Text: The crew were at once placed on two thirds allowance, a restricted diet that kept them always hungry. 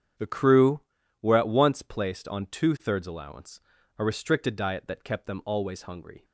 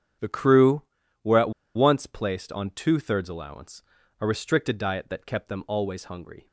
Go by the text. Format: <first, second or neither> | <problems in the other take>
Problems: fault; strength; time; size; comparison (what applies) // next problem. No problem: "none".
first | starts louder than the rest; strong; until 1.8 s; 8.5 dB; strong in the first // pauses between "at" and "once"; slight; at 1.5 s; 0.24 s long